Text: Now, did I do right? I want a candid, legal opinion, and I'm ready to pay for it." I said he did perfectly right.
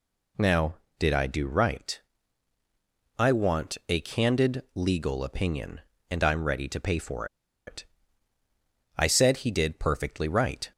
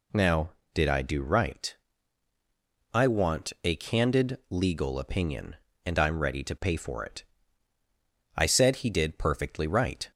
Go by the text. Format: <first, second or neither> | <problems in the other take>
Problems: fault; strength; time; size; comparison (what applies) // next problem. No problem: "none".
second | pauses between "for" and "it"; at 7.2 s; 0.40 s long